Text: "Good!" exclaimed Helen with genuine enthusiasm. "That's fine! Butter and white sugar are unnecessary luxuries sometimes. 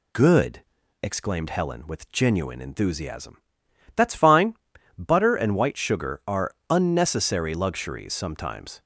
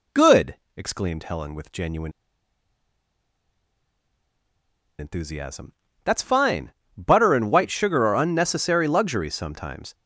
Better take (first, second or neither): first